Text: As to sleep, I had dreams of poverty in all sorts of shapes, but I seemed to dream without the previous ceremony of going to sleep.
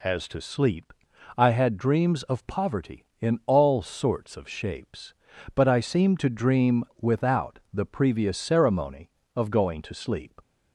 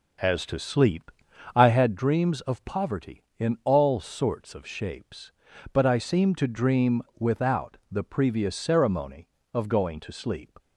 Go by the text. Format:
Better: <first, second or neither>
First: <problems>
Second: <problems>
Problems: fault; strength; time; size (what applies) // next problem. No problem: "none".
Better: first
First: pauses between "dream" and "without"; slight; at 6.8 s; 0.16 s long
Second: starts louder than the rest; noticeable; until 2.1 s; 6 dB // pauses between "dream" and "without"; slight; at 7.0 s; 0.16 s long